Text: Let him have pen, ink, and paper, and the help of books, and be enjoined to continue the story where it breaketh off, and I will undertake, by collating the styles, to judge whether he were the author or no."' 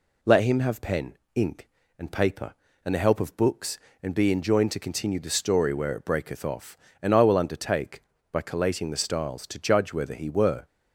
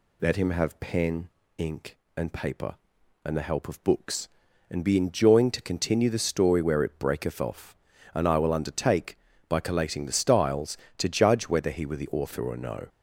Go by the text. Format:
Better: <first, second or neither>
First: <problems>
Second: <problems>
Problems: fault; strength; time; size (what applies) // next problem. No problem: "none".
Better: second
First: stops before "the author or no"; at 10.6 s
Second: none